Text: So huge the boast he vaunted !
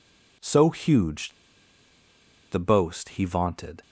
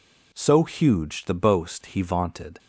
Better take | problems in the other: second | pauses between "huge" and "the"; at 1.3 s; 1.1 s long

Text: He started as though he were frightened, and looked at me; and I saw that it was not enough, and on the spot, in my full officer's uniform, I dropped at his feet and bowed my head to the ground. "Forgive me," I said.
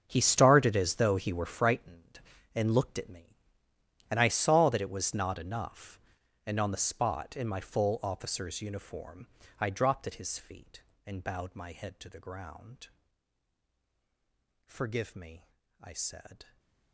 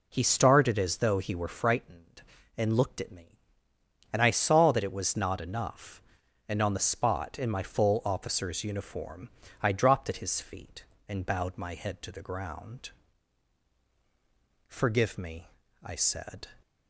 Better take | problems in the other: second | gets quieter; strong; throughout; 14.5 dB // stays silent after the last word; slight; from 16.4 s on; 0.5 s long

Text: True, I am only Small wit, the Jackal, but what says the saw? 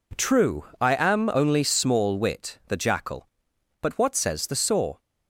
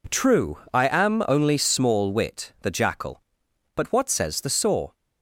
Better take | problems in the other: neither | none

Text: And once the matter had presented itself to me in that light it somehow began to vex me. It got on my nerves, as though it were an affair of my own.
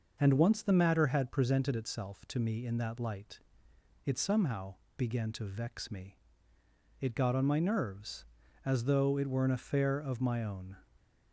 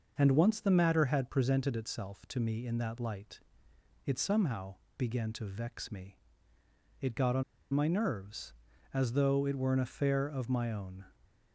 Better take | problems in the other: first | pauses between "light" and "it"; noticeable; at 3.3 s; 0.66 s long; noticeable in the first // pauses between "somehow" and "began"; slight; at 4.7 s; 0.22 s long; slight in the first // pauses between "on" and "my"; slight; at 7.4 s; 0.30 s long

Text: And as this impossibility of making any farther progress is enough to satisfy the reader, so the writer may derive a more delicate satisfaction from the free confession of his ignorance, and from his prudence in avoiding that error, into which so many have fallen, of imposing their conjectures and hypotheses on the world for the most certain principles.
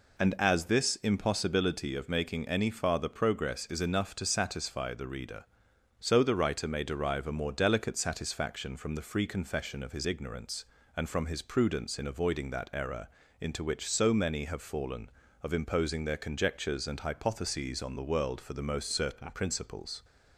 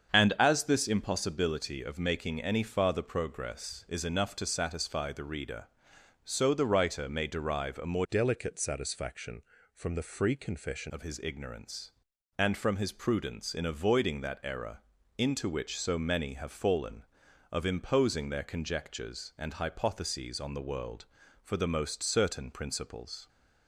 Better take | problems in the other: first | starts louder than the rest; strong; until 1.1 s; 7.5 dB // changes voice from "delicate" to "confession"; from 8.0 to 10.9 s; 2.9 s long

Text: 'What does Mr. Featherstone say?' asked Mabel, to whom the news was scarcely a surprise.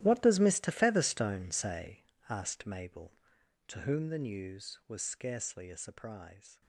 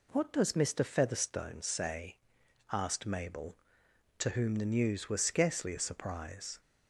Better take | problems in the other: second | gets quieter; strong; throughout; 16.5 dB

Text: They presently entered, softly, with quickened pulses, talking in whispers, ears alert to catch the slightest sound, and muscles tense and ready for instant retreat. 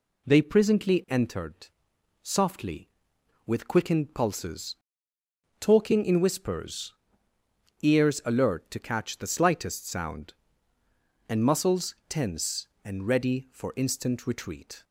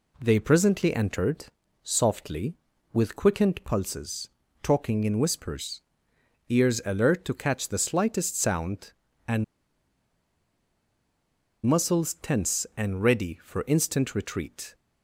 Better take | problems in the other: first | pauses between "and" and "muscles"; strong; at 9.4 s; 2.2 s long

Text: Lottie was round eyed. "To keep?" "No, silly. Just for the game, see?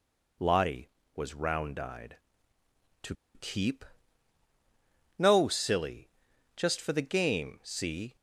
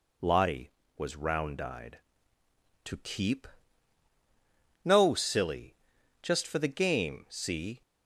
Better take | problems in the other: second | pauses between "To" and "keep"; slight; at 3.1 s; 0.19 s long

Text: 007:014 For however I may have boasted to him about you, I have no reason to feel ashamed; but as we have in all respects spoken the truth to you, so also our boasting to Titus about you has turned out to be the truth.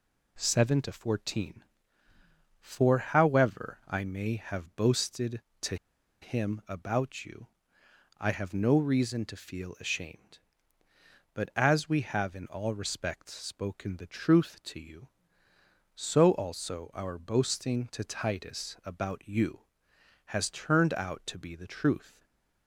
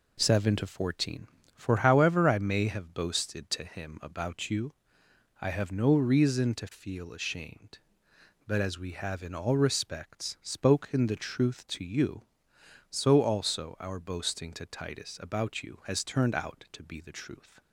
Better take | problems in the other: second | pauses between "to" and "him"; noticeable; at 5.7 s; 0.46 s long // stays silent after the last word; slight; from 22.1 s on; 0.5 s long

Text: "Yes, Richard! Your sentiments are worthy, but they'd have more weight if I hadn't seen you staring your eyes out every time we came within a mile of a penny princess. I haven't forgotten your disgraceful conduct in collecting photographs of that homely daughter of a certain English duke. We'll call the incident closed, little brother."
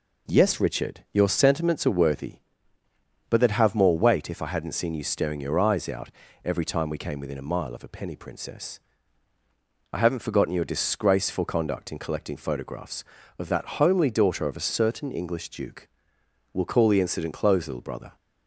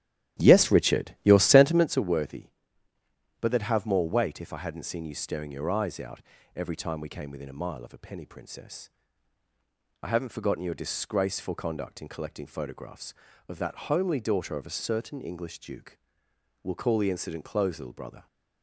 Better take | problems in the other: first | starts louder than the rest; strong; until 2.1 s; 12 dB // pauses between "out" and "every"; slight; at 6.2 s; 0.32 s long; slight in the first

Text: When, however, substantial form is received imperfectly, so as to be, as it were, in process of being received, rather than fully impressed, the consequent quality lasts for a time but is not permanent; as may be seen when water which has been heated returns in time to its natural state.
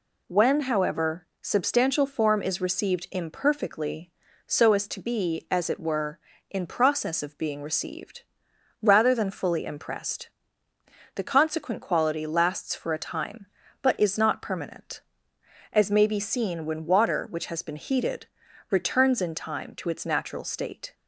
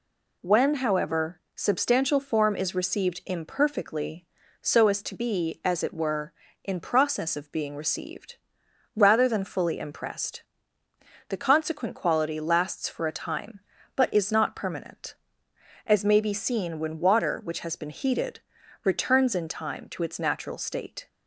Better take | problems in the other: neither | pauses between "heated" and "returns"; the same in both

